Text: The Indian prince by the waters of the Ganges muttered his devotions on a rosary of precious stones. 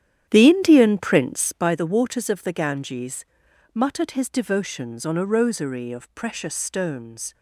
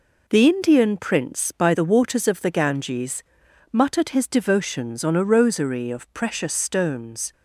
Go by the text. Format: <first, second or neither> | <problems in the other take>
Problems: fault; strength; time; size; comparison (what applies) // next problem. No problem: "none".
second | starts louder than the rest; strong; until 1.7 s; 10 dB // pauses between "Ganges" and "muttered"; noticeable; at 3.2 s; 0.50 s long; noticeable in the second